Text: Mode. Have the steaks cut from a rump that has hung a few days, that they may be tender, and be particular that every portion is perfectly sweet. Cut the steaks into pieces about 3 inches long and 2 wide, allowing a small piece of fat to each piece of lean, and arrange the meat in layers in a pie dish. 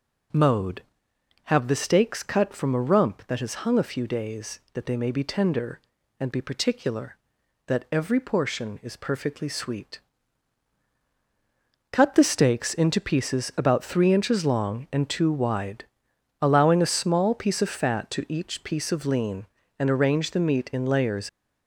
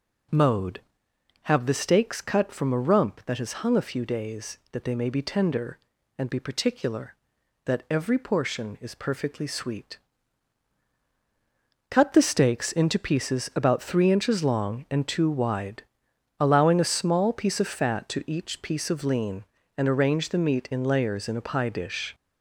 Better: second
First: stops before "in a pie dish"; at 21.2 s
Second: none

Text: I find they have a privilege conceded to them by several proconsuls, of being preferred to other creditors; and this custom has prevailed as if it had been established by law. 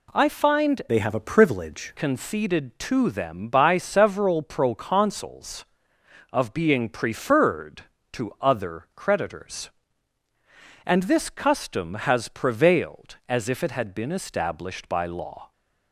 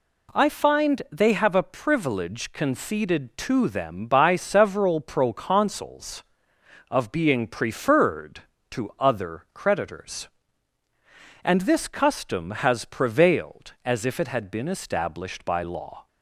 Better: second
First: changes voice from "they" to "privilege"; from 0.8 to 1.9 s; 1.1 s long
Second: none

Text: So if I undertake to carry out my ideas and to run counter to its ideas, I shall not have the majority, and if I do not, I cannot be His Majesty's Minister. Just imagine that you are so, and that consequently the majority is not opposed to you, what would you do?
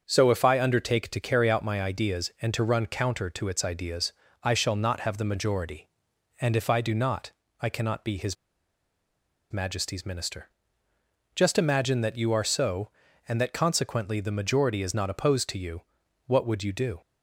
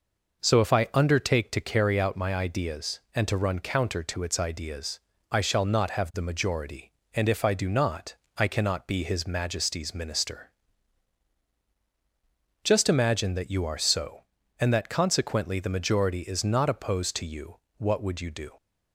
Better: second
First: starts louder than the rest; until 1.0 s; 7 dB // pauses between "His" and "Majesty's"; at 8.3 s; 1.1 s long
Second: none

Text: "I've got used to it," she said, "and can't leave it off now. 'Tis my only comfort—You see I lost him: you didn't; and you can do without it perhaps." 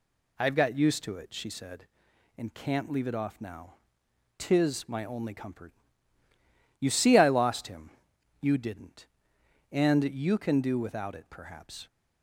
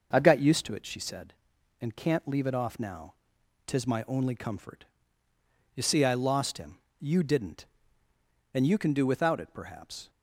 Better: neither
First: none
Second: none

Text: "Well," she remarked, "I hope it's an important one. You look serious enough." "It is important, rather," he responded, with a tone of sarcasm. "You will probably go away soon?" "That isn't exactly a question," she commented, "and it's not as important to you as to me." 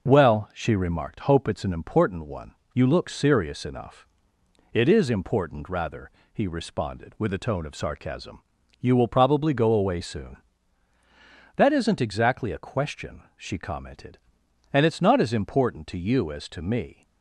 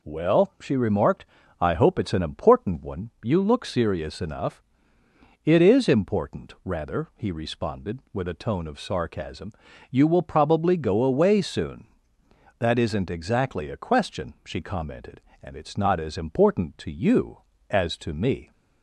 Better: second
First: skips "I"; at 1.1 s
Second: none

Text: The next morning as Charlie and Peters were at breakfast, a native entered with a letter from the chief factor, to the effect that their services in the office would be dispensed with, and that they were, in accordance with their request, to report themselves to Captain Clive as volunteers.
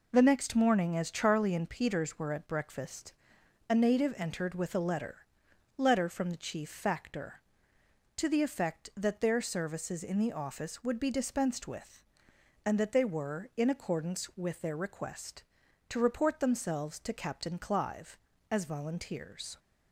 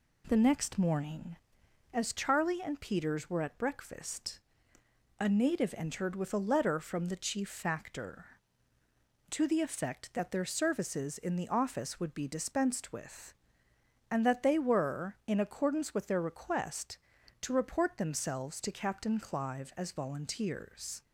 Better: second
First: says "letter" twice; at 5.7 s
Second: none

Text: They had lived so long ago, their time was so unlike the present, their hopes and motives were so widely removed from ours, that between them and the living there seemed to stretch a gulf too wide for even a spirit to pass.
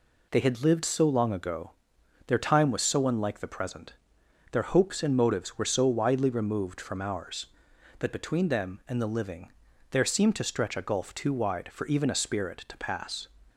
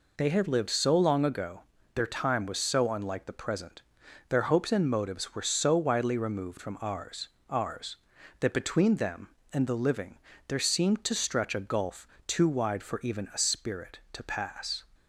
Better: first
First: pauses between "living" and "there"; at 9.5 s; 0.40 s long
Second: says "ours" twice; at 7.4 s // pauses between "living" and "there"; slight; at 10.1 s; 0.30 s long // pauses between "gulf" and "too"; slight; at 12.0 s; 0.18 s long

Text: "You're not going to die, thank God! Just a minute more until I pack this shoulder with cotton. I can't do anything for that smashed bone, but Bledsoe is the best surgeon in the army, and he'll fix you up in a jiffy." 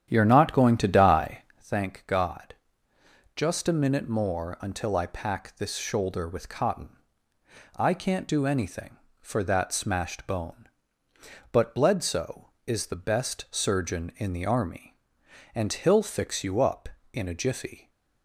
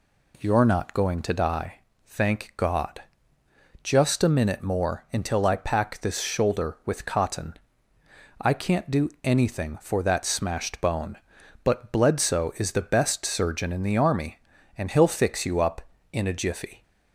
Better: second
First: starts louder than the rest; strong; until 1.7 s; 9.5 dB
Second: none

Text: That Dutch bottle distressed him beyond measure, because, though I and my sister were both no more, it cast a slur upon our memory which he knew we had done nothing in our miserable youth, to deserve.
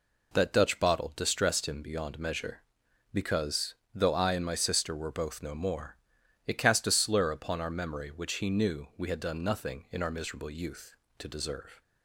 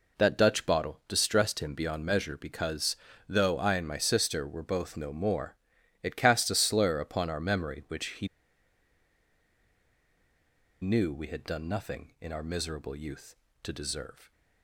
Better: first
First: none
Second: pauses between "he" and "knew"; strong; at 8.2 s; 2.5 s long

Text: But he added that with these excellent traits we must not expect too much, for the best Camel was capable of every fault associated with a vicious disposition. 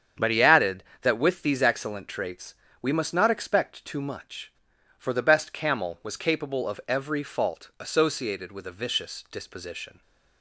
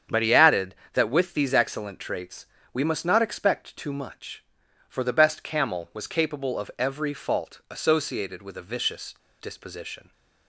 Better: first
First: starts louder than the rest; strong; until 1.3 s; 8 dB // pauses between "traits" and "we"; slight; at 2.5 s; 0.28 s long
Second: starts louder than the rest; strong; until 1.3 s; 8 dB // pauses between "traits" and "we"; slight; at 2.4 s; 0.28 s long // pauses between "vicious" and "disposition"; slight; at 9.1 s; 0.27 s long

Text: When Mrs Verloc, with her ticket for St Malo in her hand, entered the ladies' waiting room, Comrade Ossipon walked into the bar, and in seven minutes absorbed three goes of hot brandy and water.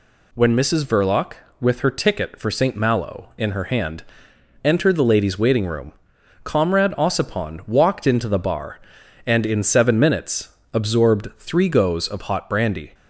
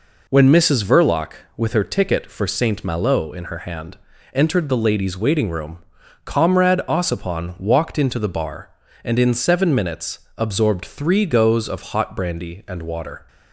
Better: second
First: pauses between "minutes" and "absorbed"; slight; at 10.5 s; 0.22 s long // stops before "and water"; at 12.9 s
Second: pauses between "minutes" and "absorbed"; slight; at 10.1 s; 0.18 s long

